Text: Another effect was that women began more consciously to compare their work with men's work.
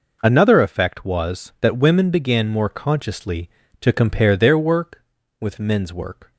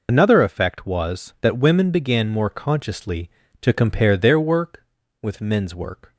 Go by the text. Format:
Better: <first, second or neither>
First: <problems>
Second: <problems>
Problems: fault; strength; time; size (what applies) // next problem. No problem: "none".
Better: first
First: none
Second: loses the start of "Another"; at 0.0 s; 75 ms